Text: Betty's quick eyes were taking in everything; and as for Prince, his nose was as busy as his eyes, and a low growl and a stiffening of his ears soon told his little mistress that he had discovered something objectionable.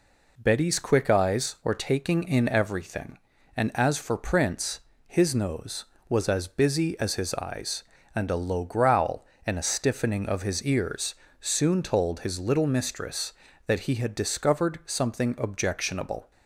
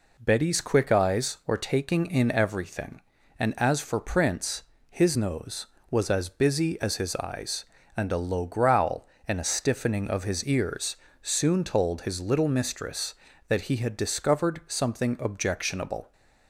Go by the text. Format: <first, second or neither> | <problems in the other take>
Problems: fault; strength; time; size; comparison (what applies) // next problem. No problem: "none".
neither | pauses between "ears" and "soon"; slight; the same in both